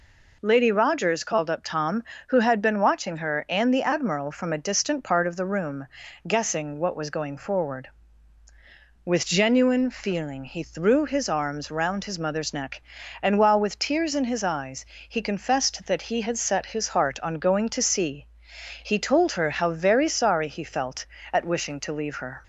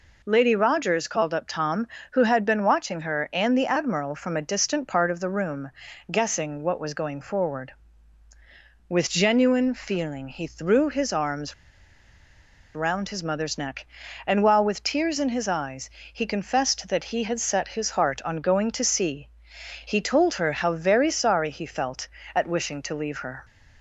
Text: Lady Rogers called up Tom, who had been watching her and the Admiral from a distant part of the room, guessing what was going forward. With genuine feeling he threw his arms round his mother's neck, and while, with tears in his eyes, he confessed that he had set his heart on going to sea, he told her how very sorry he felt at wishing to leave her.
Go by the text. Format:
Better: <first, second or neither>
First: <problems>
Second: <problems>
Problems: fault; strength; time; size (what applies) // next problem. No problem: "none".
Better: first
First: none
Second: pauses between "arms" and "round"; at 11.5 s; 1.2 s long